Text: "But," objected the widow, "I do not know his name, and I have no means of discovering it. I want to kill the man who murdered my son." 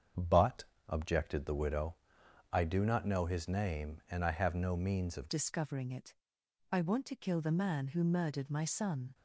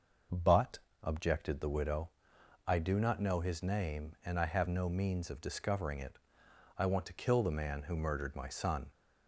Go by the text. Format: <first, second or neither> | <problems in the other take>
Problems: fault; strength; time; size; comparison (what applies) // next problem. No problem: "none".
second | starts louder than the rest; strong; until 1.4 s; 7.5 dB // changes voice at "discovering"; from 5.2 s on; 3.9 s long